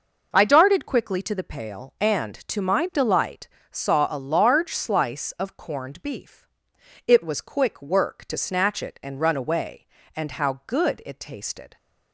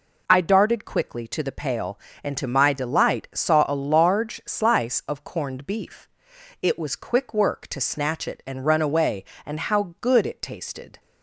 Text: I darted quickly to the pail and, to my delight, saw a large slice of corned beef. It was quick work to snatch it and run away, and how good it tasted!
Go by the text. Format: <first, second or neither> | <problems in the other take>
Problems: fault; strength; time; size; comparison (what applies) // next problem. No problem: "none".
neither | none